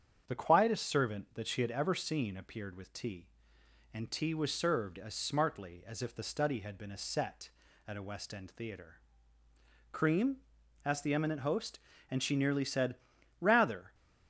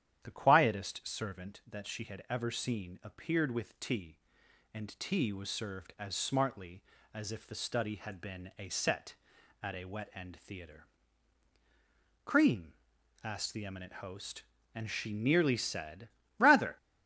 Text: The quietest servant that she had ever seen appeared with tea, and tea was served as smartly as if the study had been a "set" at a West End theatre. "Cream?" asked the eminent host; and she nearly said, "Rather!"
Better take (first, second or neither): first